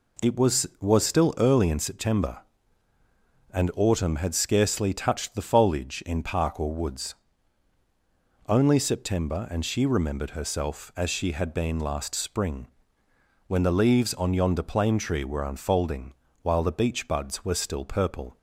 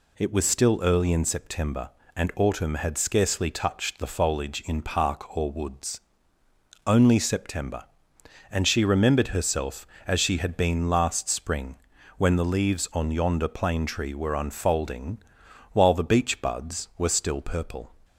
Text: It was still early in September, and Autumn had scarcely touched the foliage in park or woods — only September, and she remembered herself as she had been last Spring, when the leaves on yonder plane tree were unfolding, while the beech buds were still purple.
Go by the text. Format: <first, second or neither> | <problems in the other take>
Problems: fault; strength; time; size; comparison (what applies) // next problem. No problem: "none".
second | says "was" twice; at 0.7 s